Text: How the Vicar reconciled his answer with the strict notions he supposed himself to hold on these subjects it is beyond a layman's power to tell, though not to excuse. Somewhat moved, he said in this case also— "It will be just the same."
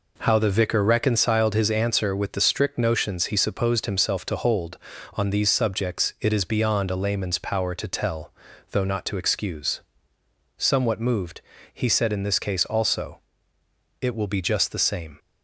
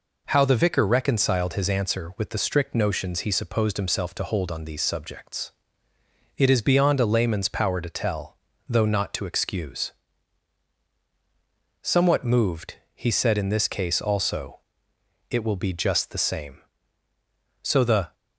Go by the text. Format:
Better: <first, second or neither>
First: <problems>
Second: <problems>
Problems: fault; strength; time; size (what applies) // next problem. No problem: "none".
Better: first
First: none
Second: pauses between "subjects" and "it"; noticeable; at 5.5 s; 0.84 s long // goes on to say "So the"; from 17.6 s on; 0.52 s long